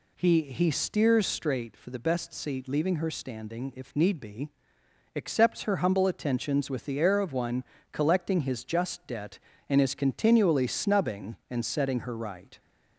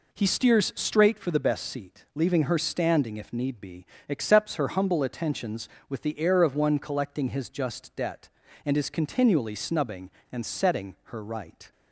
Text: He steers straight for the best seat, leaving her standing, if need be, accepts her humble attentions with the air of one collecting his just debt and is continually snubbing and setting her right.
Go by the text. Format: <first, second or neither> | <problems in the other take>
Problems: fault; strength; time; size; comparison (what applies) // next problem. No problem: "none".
second | says "He" twice; at 0.4 s // pauses between "one" and "collecting"; slight; at 7.6 s; 0.26 s long